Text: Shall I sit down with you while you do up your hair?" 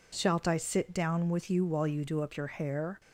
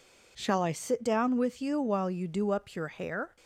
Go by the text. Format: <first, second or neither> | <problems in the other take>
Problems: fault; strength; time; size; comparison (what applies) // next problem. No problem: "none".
second | says "Shalt" for "Shall"; at 0.1 s